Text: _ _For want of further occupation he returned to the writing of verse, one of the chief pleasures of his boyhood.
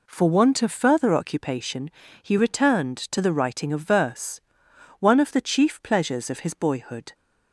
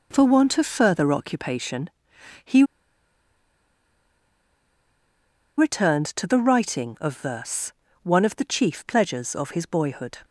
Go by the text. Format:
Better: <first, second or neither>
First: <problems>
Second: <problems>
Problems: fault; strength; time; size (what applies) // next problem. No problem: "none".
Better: first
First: pauses between "occupation" and "he"; slight; at 1.9 s; 0.32 s long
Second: pauses between "occupation" and "he"; noticeable; at 1.8 s; 0.54 s long // pauses between "he" and "returned"; strong; at 2.6 s; 2.9 s long